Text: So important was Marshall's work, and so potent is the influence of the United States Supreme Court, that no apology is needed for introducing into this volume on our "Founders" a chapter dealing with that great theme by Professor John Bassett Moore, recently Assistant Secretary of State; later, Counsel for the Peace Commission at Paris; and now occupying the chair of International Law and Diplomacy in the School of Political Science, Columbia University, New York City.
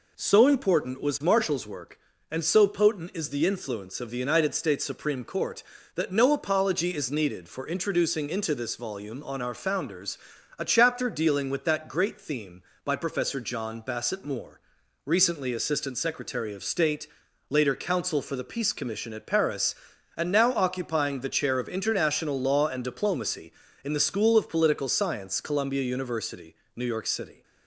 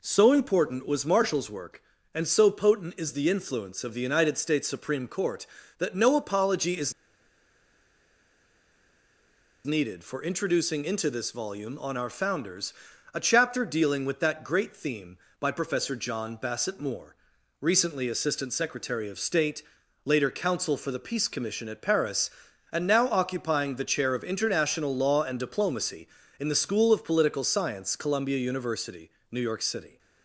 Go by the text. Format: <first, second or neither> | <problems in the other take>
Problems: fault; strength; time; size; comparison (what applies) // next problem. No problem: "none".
first | pauses between "is" and "needed"; strong; at 6.9 s; 2.7 s long // pauses between "Founders" and "a"; at 12.7 s; 0.40 s long; also in the first